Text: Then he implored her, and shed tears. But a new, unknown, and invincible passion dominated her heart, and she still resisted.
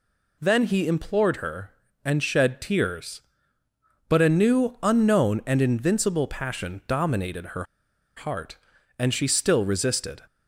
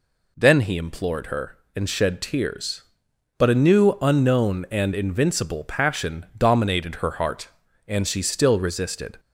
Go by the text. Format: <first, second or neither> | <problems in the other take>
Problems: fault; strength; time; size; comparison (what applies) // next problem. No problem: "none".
second | pauses between "her" and "heart"; noticeable; at 7.6 s; 0.52 s long